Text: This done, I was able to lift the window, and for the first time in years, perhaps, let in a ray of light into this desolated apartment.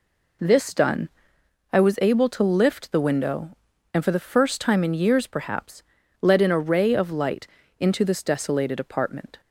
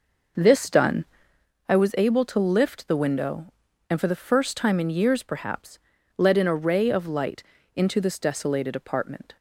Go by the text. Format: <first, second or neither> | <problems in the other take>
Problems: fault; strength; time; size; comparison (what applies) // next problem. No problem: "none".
first | starts louder than the rest; noticeable; until 1.6 s; 5.5 dB // pauses between "light" and "into"; slight; at 7.4 s; 0.32 s long; slight in the first